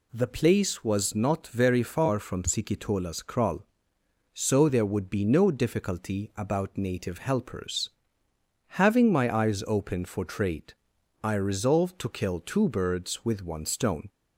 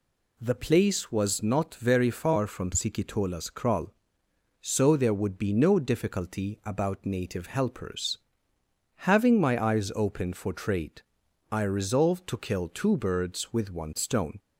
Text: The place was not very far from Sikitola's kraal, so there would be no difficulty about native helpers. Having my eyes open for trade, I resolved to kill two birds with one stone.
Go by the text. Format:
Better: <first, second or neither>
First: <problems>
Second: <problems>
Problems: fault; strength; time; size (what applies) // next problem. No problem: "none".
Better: neither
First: none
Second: none